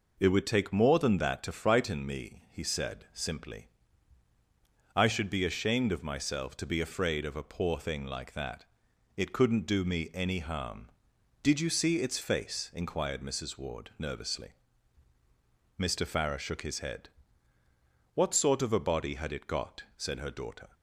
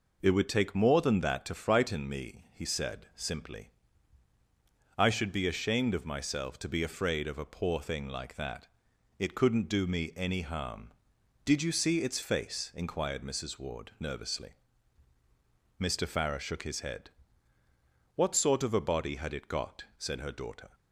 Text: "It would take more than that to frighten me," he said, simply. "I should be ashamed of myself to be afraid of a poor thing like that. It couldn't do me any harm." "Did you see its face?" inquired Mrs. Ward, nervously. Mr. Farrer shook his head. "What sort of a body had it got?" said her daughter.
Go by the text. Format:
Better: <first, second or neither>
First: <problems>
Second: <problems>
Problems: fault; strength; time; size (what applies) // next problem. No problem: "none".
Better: neither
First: none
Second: none